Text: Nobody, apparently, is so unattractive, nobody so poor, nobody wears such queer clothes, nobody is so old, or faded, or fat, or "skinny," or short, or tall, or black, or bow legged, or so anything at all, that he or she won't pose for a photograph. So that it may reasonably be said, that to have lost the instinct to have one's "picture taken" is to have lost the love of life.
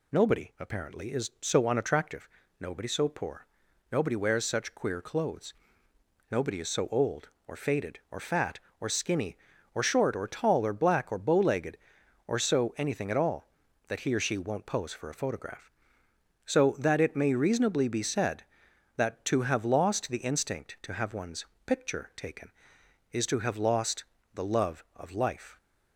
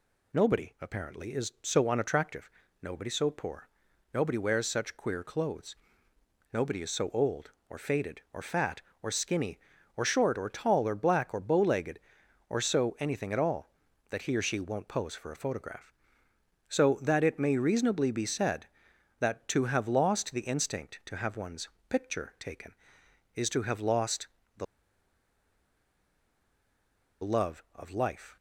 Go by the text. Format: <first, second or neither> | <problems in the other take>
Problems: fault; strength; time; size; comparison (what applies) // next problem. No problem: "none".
first | pauses between "one's" and "picture"; slight; at 21.7 s; 0.18 s long; slight in the first // pauses between "lost" and "the"; slight; at 24.2 s; 0.32 s long; slight in the first // pauses between "the" and "love"; strong; at 24.6 s; 2.5 s long